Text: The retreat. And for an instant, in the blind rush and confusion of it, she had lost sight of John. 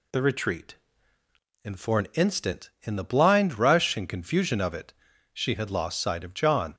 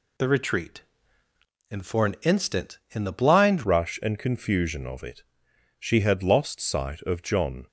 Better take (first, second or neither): first